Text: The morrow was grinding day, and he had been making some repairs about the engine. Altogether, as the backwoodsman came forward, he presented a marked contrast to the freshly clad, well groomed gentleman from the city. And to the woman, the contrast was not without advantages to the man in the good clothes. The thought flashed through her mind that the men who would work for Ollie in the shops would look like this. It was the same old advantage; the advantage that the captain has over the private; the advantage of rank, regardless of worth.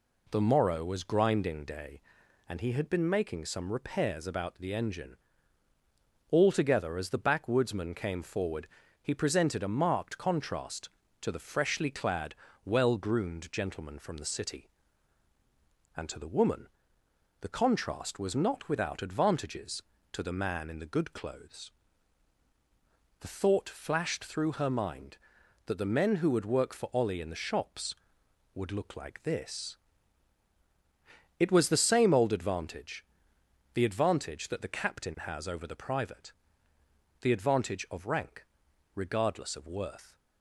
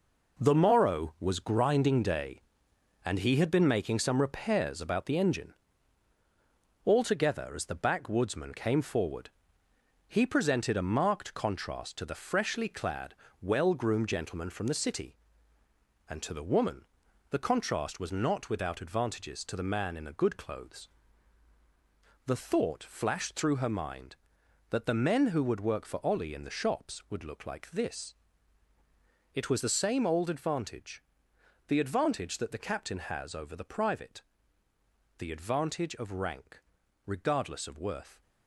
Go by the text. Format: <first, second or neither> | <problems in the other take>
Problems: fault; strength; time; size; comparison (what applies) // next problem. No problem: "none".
first | gets quieter; strong; throughout; 7.5 dB